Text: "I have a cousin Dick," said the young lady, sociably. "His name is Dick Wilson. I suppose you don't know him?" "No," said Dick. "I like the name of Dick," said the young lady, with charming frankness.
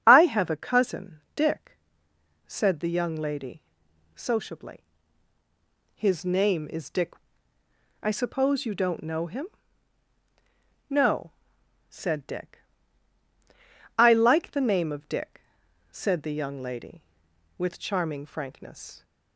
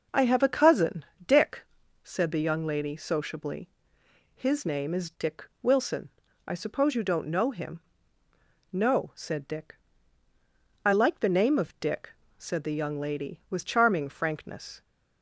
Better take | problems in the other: second | starts louder than the rest; strong; until 1.0 s; 7 dB // pauses between "cousin" and "Dick"; slight; at 1.1 s; 0.16 s long; slight in the second // skips "Wilson"; at 7.6 s

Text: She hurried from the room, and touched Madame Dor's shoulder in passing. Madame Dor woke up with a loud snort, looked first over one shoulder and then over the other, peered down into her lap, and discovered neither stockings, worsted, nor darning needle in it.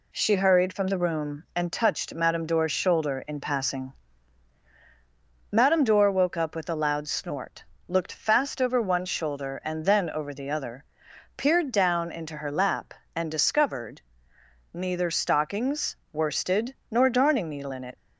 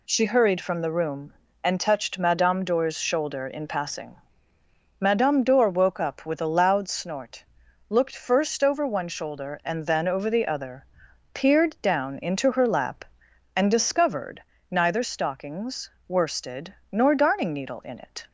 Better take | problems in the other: second | says "fast" for "first"; at 8.1 s // pauses between "discovered" and "neither"; noticeable; at 14.0 s; 0.72 s long; slight in the second

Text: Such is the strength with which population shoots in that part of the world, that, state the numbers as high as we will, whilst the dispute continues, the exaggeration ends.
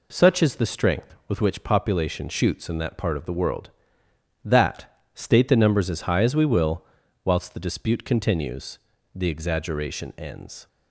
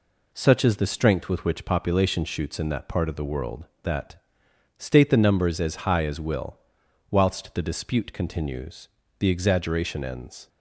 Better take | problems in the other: first | skips "we"; at 6.1 s

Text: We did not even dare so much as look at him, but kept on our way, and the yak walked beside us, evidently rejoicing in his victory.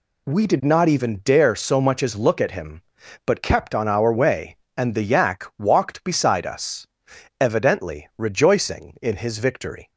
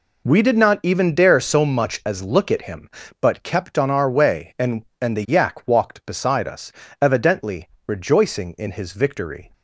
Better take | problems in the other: first | says "and" twice; at 5.0 s // pauses between "evidently" and "rejoicing"; slight; at 7.6 s; 0.18 s long

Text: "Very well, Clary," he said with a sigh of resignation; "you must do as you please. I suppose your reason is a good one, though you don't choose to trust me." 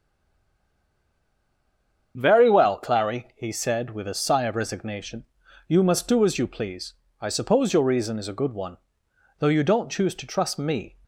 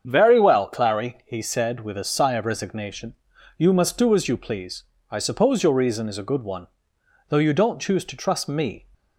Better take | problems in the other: second | stays silent before the first word; until 2.1 s; 2.1 s long // starts louder than the rest; strong; until 3.1 s; 7.5 dB; strong in the second

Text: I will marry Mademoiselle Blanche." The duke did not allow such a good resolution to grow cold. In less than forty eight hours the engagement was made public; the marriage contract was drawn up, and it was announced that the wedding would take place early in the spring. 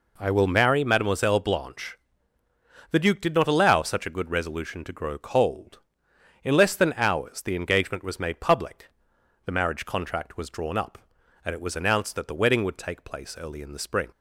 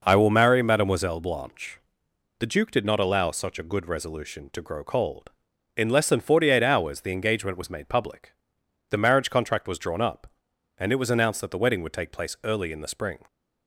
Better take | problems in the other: second | skips "forty eight"; at 6.9 s

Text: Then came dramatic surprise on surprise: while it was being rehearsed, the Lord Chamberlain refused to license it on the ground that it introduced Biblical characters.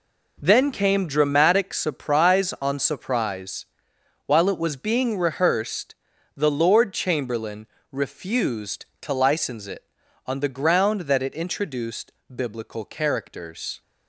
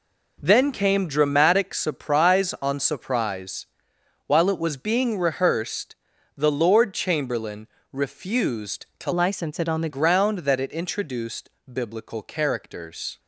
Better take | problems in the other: first | pauses between "Chamberlain" and "refused"; slight; at 7.6 s; 0.24 s long; slight in the first // changes voice from "license" to "the"; from 9.1 to 9.8 s; 0.7 s long // pauses between "introduced" and "Biblical"; slight; at 11.4 s; 0.16 s long; slight in the first

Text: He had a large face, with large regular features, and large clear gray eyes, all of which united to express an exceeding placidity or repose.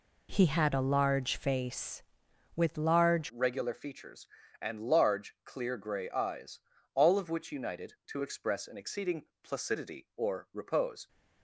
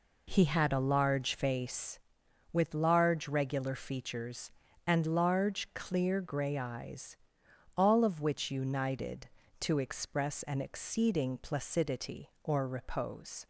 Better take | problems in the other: second | changes voice at "regular"; from 3.2 s on; 7.8 s long // pauses between "exceeding" and "placidity"; slight; at 9.2 s; 0.16 s long

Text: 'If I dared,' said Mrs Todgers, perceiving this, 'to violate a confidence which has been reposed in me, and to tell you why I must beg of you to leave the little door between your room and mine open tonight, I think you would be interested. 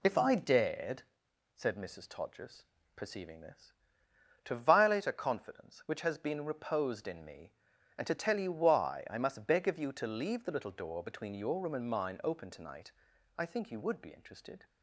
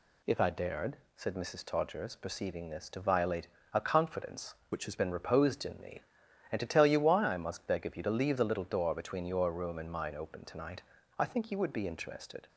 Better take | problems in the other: first | pauses between "violate" and "a"; slight; at 3.4 s; 0.26 s long // changes voice from "which" to "has"; from 4.7 to 4.9 s; 0.2 s long

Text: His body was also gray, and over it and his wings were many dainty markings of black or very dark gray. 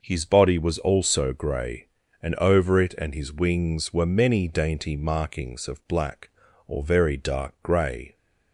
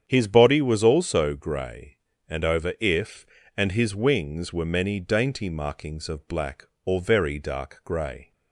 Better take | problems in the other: first | starts louder than the rest; strong; until 1.0 s; 8.5 dB // says "if" for "it"; at 2.7 s

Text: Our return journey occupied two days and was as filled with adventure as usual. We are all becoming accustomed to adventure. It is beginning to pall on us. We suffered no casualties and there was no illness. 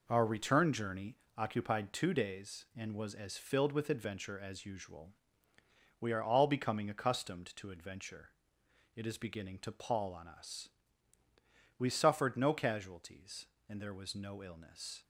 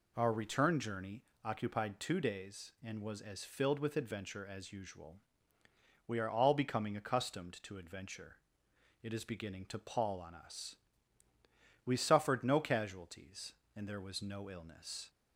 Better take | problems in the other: second | gets quieter; throughout; 7 dB // pauses between "journey" and "occupied"; slight; at 1.1 s; 0.20 s long; slight in the second

